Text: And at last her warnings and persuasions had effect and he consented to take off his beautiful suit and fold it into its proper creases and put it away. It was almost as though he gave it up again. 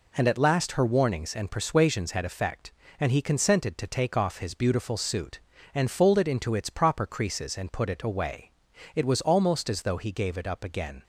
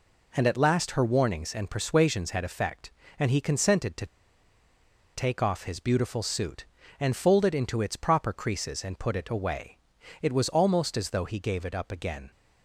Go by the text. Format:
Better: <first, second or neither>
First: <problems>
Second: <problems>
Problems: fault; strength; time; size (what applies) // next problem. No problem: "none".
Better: first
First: none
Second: pauses between "to" and "take"; at 4.0 s; 1.0 s long